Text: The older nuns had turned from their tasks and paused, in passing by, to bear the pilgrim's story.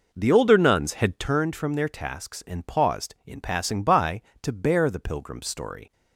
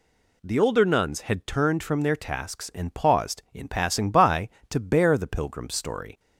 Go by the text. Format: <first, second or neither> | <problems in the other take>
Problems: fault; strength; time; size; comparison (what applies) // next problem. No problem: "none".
second | starts louder than the rest; noticeable; until 1.5 s; 5 dB